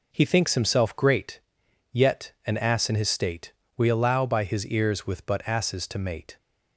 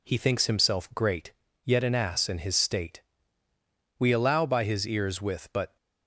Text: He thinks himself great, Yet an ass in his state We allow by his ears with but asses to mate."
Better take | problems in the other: first | pauses between "state" and "We"; noticeable; at 3.0 s; 0.96 s long; slight in the first // stops before "asses to mate"; at 5.7 s

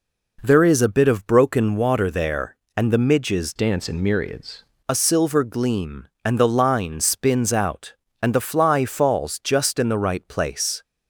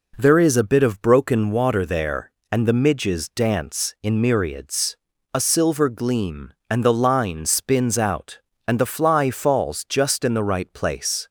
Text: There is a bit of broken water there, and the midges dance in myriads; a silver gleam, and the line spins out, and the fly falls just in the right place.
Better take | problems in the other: second | changes voice from "dance" to "myriads"; from 3.5 to 4.6 s; 1.1 s long

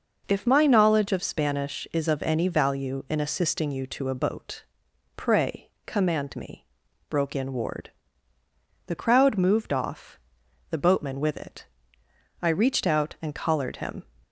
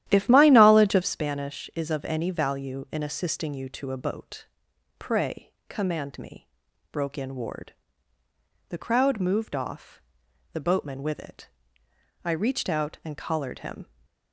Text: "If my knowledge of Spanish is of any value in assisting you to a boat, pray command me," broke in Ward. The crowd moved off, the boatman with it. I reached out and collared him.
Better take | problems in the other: first | starts louder than the rest; strong; until 1.2 s; 12 dB // pauses between "pray" and "command"; slight; at 5.5 s; 0.16 s long; slight in the first

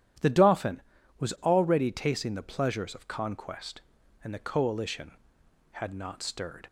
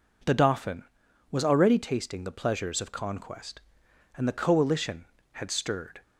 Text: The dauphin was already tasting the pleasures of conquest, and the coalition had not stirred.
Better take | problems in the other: first | skips "not"; at 5.4 s

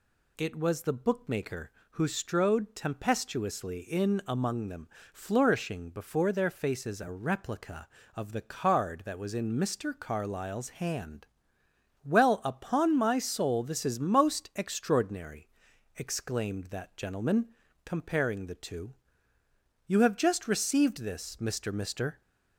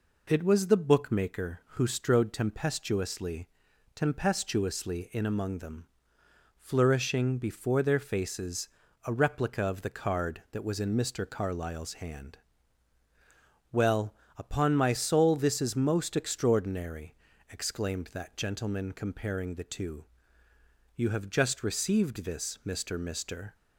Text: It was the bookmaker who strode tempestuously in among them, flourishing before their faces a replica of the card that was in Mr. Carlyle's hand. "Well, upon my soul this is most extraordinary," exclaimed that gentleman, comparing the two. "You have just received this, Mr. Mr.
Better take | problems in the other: first | says "tempestuously" twice; at 3.9 s // pauses between "faces" and "a"; at 8.6 s; 0.38 s long

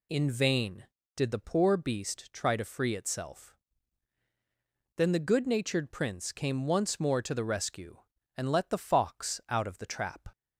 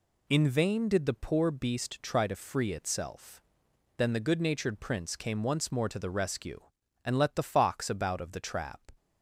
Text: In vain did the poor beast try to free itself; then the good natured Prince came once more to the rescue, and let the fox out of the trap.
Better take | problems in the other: first | says "about" for "out"; at 7.8 s

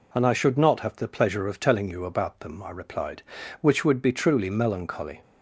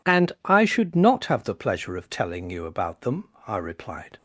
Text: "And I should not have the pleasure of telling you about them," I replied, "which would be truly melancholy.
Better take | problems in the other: first | stops before "which would be truly melancholy"; at 4.1 s

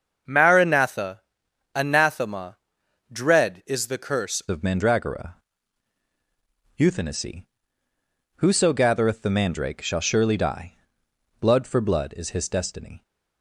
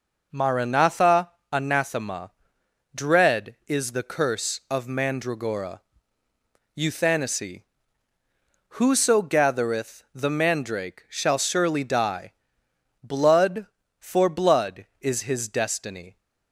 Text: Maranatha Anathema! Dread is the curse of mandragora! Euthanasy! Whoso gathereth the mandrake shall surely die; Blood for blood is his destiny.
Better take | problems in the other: second | starts louder than the rest; until 1.8 s; 7 dB // pauses between "Maranatha" and "Anathema"; noticeable; at 1.2 s; 0.54 s long; slight in the second // changes voice at "of"; from 4.4 s on; 8.6 s long

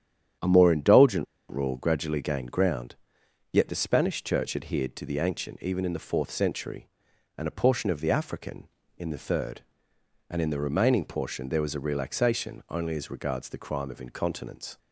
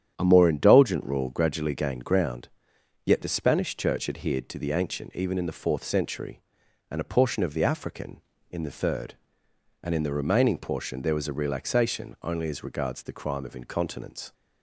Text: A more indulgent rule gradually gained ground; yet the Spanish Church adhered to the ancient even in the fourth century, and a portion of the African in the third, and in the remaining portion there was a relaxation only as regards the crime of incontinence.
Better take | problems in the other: second | starts louder than the rest; strong; until 1.6 s; 9.5 dB; strong in the second // pauses between "indulgent" and "rule"; slight; at 1.2 s; 0.24 s long

